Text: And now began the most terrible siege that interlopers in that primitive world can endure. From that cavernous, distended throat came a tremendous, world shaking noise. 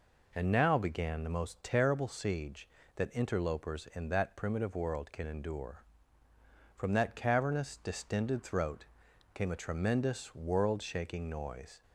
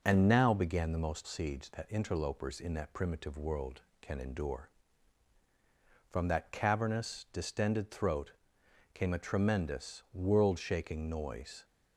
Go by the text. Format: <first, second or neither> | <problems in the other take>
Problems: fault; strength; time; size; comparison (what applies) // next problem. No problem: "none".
first | skips "terrible"; at 1.2 s // pauses between "throat" and "came"; noticeable; at 8.3 s; 0.60 s long; noticeable in the first